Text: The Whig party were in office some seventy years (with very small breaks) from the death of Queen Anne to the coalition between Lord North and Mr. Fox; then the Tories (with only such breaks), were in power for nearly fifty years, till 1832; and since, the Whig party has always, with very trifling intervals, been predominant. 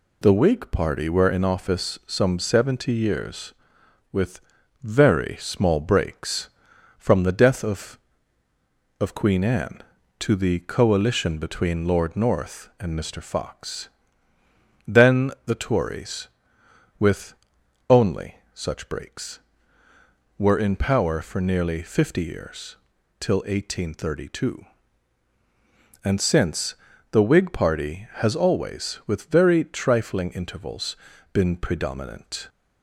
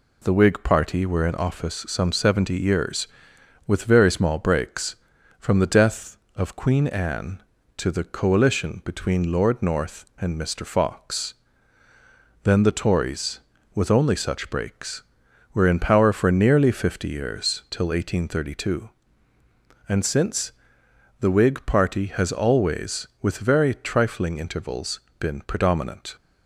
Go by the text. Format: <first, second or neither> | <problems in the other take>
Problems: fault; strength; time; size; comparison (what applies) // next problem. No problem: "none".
second | pauses between "with" and "very"; at 4.3 s; 0.42 s long // says "of" twice; at 9.0 s // pauses between "with" and "only"; noticeable; at 17.3 s; 0.56 s long // pauses between "only" and "such"; slight; at 18.3 s; 0.18 s long